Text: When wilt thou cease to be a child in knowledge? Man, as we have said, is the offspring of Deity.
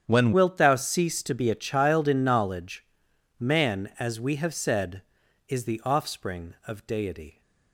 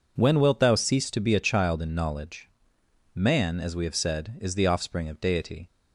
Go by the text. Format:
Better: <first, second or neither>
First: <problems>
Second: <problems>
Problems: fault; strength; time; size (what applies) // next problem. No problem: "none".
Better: second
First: starts louder than the rest; strong; until 1.0 s; 8.5 dB // changes voice at "wilt"; from 0.3 s on; 7.1 s long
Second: none